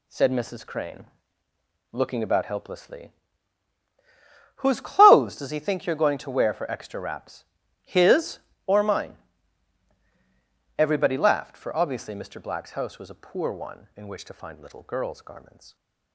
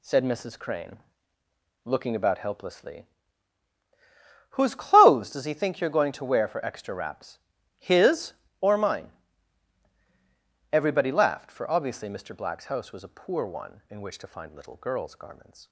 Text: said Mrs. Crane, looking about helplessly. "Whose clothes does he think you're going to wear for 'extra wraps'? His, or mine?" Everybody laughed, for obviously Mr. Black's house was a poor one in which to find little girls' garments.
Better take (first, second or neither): neither